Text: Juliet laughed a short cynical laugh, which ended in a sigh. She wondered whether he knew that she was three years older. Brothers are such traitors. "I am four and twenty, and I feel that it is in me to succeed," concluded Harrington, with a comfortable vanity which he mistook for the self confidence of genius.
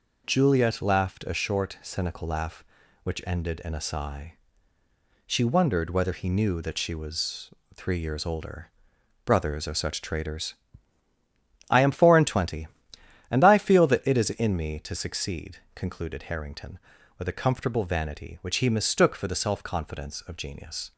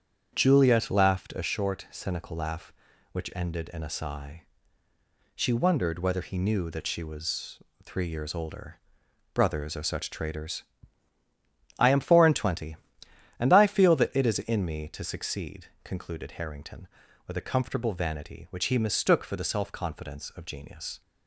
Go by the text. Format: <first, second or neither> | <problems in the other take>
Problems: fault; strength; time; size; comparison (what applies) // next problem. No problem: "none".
first | starts louder than the rest; strong; until 1.4 s; 8 dB // pauses between "was" and "three"; slight; at 7.5 s; 0.24 s long; slight in the first